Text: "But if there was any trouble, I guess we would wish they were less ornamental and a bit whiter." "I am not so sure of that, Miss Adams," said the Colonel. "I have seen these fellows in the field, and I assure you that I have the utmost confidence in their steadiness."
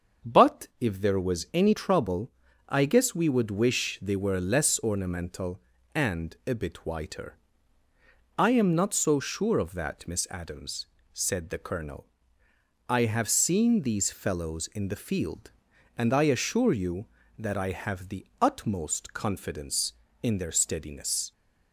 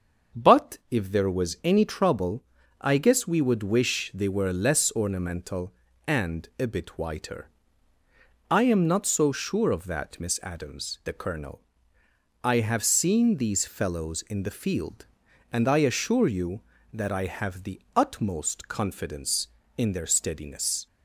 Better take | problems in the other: first | starts louder than the rest; until 1.4 s; 6.5 dB; also in the first // skips "said"; at 11.0 s // pauses between "the" and "utmost"; slight; at 17.8 s; 0.16 s long; slight in the first

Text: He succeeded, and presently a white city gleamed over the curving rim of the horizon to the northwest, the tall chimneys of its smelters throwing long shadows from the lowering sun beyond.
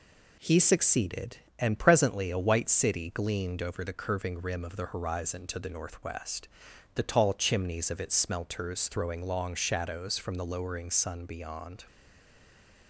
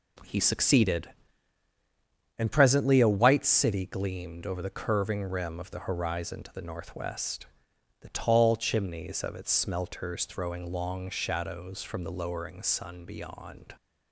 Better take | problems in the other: second | stays silent after the last word; from 11.8 s on; 1.0 s long

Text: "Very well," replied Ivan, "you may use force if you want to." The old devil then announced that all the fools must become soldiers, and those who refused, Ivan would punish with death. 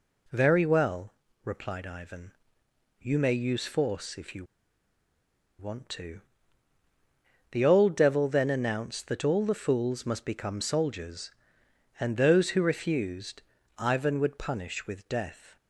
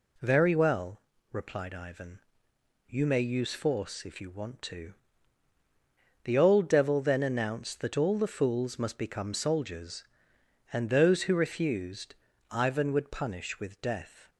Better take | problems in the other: second | pauses between "you" and "want"; at 4.4 s; 1.1 s long

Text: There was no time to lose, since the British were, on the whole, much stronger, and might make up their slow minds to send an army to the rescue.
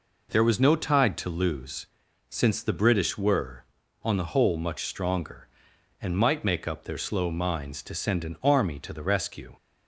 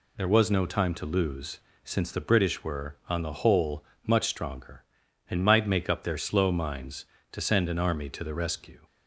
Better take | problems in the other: second | says "tide" for "time"; at 0.7 s

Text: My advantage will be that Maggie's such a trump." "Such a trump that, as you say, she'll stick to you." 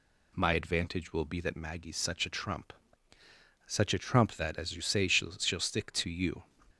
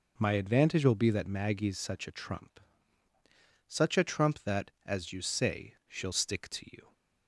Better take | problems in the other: second | says "she'll" twice; at 5.3 s

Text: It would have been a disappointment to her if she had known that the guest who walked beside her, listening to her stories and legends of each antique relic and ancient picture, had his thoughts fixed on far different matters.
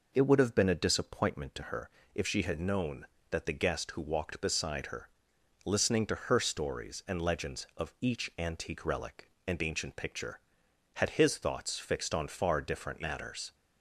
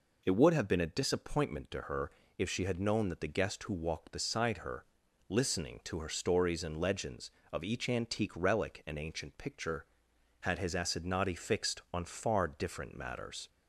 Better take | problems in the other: first | pauses between "her" and "if"; slight; at 2.1 s; 0.28 s long; slight in the first // says "assignati" for "thoughts"; at 10.7 s

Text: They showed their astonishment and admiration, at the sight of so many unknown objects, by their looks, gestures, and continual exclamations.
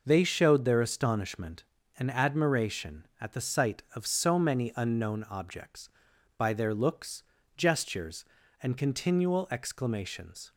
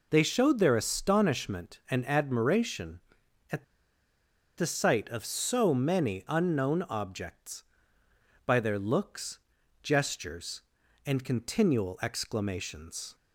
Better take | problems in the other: first | pauses between "at" and "the"; noticeable; at 3.6 s; 0.92 s long

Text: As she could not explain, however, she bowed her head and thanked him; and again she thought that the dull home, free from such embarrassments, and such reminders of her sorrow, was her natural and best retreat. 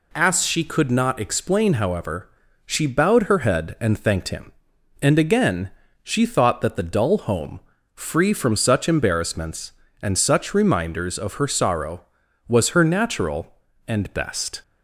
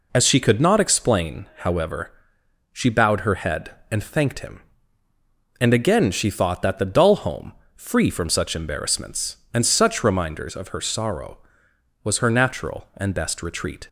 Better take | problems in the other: second | pauses between "again" and "she"; slight; at 5.6 s; 0.32 s long // stops before "retreat"; at 14.6 s

